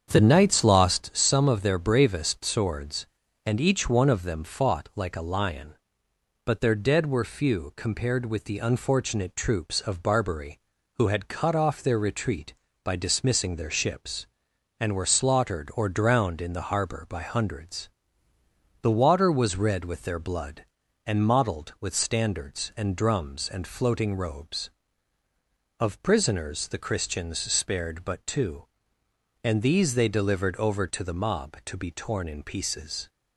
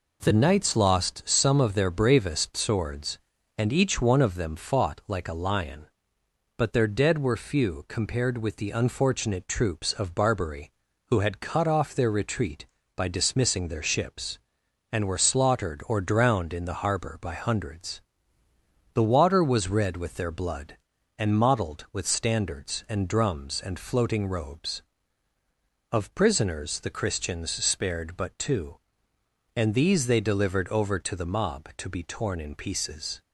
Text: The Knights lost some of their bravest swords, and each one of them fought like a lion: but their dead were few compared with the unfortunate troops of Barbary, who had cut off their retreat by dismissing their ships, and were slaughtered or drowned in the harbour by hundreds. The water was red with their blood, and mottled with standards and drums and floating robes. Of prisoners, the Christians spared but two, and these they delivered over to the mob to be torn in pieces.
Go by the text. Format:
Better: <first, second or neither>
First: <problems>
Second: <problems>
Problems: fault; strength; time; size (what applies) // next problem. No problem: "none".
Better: second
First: starts louder than the rest; strong; until 1.2 s; 7.5 dB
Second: none